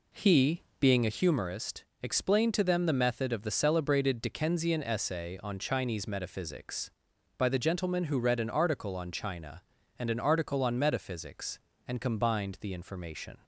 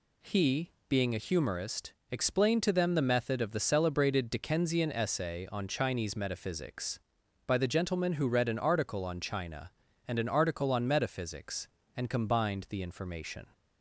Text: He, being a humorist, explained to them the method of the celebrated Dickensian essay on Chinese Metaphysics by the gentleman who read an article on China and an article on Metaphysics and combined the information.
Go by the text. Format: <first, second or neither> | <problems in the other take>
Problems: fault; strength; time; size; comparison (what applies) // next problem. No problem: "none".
second | starts louder than the rest; slight; until 1.4 s; 3.5 dB